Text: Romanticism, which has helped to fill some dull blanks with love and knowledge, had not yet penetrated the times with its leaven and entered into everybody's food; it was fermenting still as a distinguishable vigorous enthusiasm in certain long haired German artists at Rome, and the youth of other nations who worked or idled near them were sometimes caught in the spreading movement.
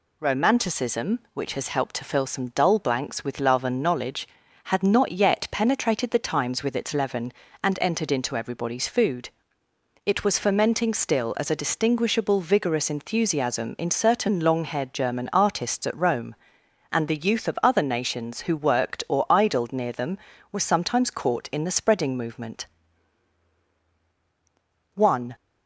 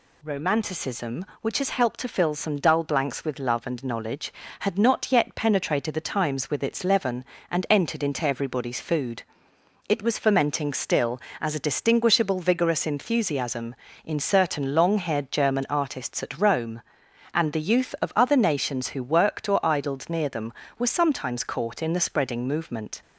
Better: second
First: goes on to say "One"; slight; from 24.9 s on; 0.42 s long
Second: none

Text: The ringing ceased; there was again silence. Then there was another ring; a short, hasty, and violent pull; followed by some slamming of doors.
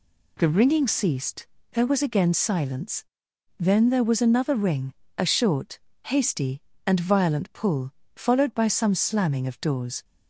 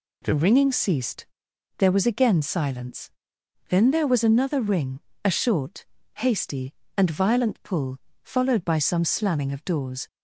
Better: neither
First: none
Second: none

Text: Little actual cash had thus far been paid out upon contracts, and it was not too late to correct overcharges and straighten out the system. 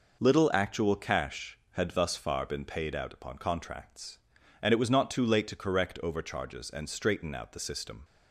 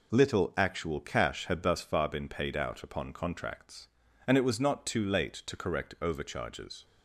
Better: first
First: none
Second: stops before "and straighten out the system"; at 6.8 s

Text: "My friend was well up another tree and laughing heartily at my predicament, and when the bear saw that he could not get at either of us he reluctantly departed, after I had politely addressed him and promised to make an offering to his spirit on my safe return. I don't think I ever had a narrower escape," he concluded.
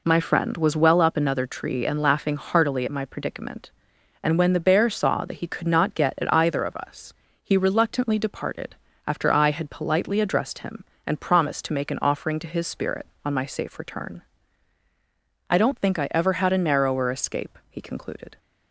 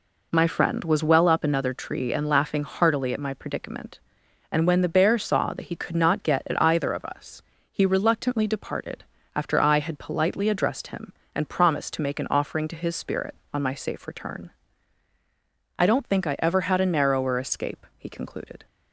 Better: neither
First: pauses between "us" and "he"; slight; at 7.1 s; 0.30 s long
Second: pauses between "us" and "he"; slight; at 7.4 s; 0.30 s long

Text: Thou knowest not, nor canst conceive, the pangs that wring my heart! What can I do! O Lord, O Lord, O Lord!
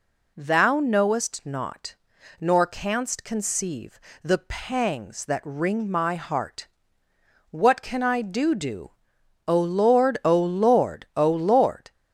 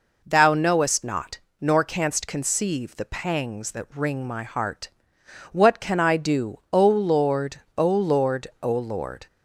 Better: second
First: says "do" twice; at 8.5 s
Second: none

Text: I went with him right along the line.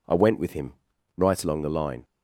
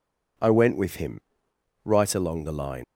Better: first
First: pauses between "him" and "right"; at 0.7 s; 0.42 s long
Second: pauses between "him" and "right"; noticeable; at 1.1 s; 0.64 s long // leaves "line" unfinished; at 2.8 s; 125 ms

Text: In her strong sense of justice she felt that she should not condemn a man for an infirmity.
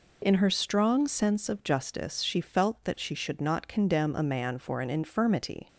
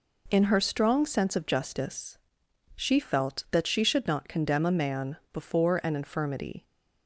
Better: first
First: none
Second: pauses between "justice" and "she"; noticeable; at 2.1 s; 0.58 s long // says "before" for "for"; at 5.3 s

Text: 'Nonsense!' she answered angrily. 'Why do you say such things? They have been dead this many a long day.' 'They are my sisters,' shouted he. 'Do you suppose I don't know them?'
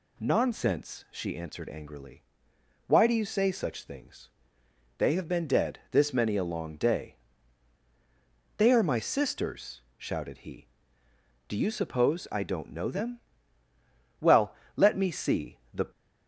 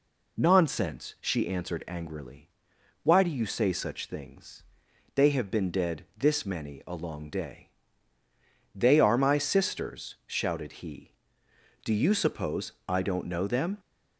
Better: second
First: goes on to say "Well let me see the"; strong; from 14.1 s on; 1.7 s long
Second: none

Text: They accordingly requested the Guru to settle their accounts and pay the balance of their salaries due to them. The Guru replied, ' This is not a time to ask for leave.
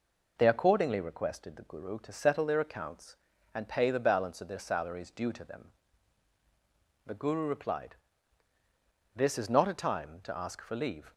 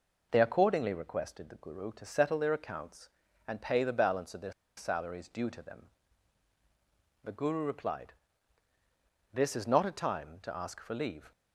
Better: first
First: none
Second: pauses between "their" and "salaries"; slight; at 4.5 s; 0.25 s long

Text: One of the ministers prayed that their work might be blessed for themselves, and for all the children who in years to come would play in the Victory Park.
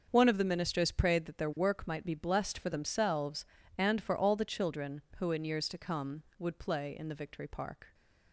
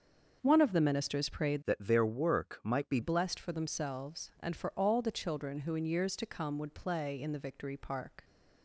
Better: first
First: starts louder than the rest; until 1.1 s; 6.5 dB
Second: starts louder than the rest; until 1.4 s; 6.5 dB // changes voice from "that" to "be"; from 1.6 to 2.9 s; 1.3 s long

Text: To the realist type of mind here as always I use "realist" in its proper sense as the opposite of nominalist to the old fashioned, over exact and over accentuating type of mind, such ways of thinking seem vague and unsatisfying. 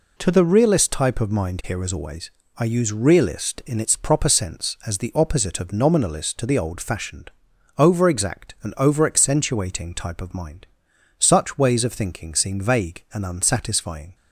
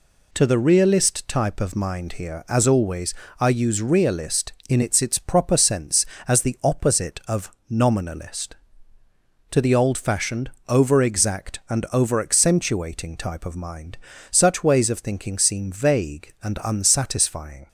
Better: first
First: pauses between "always" and "I"; slight; at 2.3 s; 0.26 s long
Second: pauses between "always" and "I"; slight; at 3.1 s; 0.28 s long // says "its" twice; at 5.0 s // pauses between "of" and "nominalist"; slight; at 7.4 s; 0.20 s long

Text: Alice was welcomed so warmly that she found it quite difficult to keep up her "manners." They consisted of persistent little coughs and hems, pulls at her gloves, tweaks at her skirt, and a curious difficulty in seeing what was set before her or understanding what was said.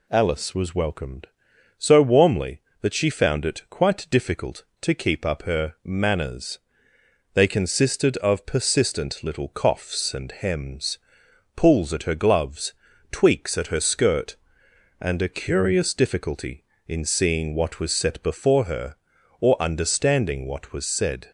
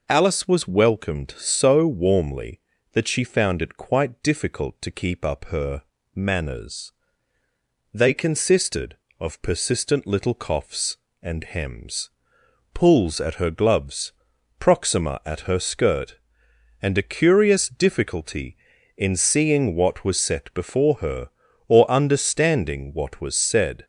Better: first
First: none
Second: pauses between "her" and "manners"; slight; at 5.8 s; 0.32 s long // says "proxima" for "tweaks"; at 14.5 s

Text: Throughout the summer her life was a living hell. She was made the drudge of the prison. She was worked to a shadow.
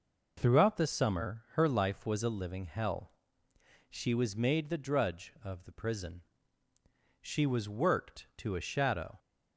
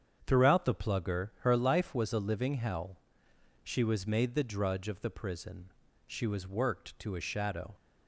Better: first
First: none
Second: starts louder than the rest; strong; until 1.2 s; 8 dB // says "plugger" for "summer"; at 0.7 s

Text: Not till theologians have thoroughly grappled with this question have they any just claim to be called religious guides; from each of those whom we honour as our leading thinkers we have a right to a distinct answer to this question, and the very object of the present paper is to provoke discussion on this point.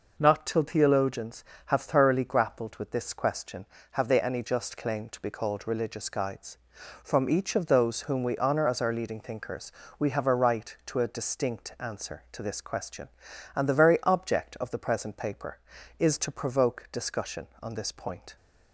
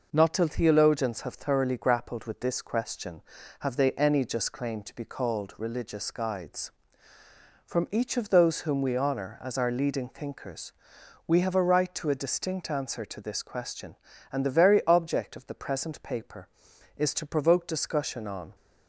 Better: first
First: pauses between "thinkers" and "we"; slight; at 9.7 s; 0.26 s long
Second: pauses between "thinkers" and "we"; noticeable; at 10.7 s; 0.54 s long // stops before "this point"; at 18.5 s

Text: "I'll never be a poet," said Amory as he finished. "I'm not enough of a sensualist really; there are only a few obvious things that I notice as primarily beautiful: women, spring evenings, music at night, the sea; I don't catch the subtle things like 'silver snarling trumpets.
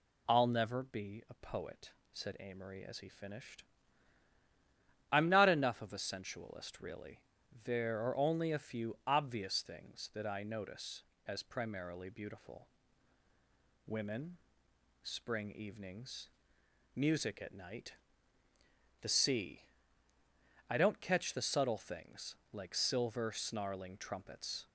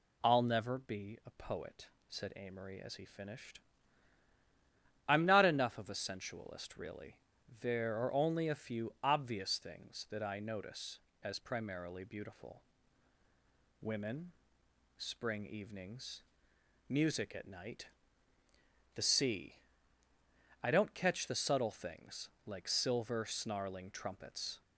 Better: neither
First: pauses between "things" and "like"; slight; at 22.3 s; 0.16 s long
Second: pauses between "things" and "like"; slight; at 22.2 s; 0.16 s long

